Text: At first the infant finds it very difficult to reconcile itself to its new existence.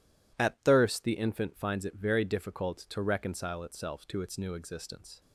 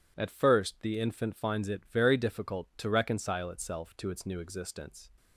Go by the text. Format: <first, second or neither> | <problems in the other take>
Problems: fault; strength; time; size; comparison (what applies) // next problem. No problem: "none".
second | says "thirst" for "first"; at 0.6 s